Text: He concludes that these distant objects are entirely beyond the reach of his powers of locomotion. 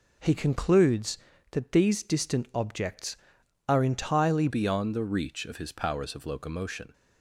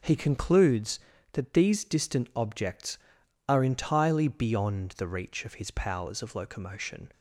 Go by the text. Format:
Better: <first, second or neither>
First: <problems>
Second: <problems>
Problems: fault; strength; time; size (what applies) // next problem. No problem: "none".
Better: second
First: changes voice at "beyond"; from 4.4 s on; 2.5 s long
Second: none